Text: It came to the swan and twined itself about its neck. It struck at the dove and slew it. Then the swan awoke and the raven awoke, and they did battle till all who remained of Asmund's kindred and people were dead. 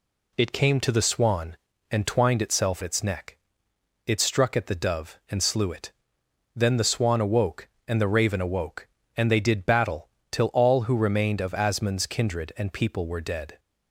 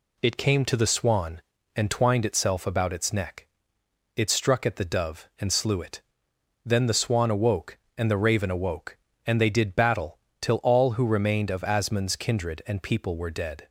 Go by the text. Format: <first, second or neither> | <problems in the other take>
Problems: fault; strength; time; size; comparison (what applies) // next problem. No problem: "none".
second | skips "about"; at 2.8 s // pauses between "battle" and "till"; slight; at 10.0 s; 0.22 s long; slight in the second